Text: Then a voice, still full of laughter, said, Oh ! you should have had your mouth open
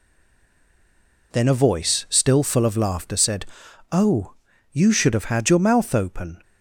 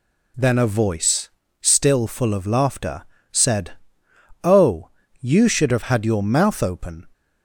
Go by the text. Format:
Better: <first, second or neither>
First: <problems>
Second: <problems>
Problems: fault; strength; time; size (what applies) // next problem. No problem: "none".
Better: second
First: stays silent before the first word; noticeable; until 1.3 s; 1.3 s long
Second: none